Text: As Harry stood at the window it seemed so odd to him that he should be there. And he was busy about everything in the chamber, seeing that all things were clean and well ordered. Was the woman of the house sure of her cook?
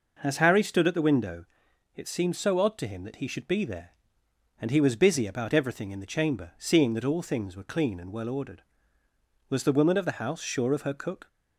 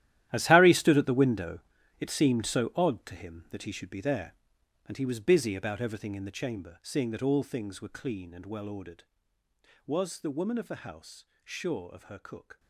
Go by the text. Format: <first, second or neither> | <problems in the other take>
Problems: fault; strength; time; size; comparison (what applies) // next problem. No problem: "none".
first | gets quieter; strong; throughout; 15 dB // pauses between "window" and "it"; at 1.5 s; 0.40 s long; noticeable in the first // pauses between "house" and "sure"; slight; at 11.2 s; 0.18 s long